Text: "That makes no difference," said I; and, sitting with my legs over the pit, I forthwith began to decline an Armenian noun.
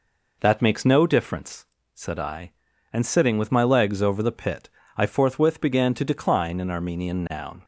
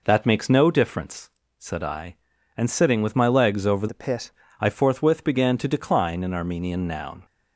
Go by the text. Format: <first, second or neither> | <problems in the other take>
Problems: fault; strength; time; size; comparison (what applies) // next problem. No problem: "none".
first | changes voice from "the" to "pit"; from 3.8 to 4.3 s; 0.5 s long